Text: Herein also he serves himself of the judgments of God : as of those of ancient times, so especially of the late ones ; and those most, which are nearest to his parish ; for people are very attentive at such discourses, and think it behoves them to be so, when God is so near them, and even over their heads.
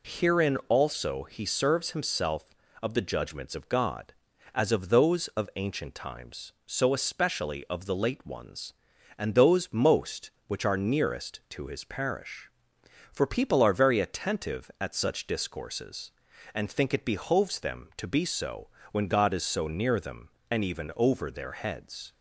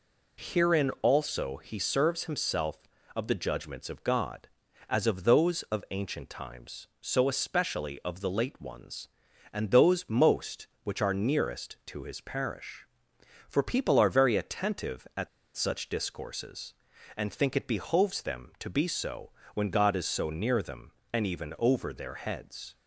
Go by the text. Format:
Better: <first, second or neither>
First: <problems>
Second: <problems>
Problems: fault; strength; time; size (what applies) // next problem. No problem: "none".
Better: first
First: none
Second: pauses between "at" and "such"; slight; at 15.2 s; 0.26 s long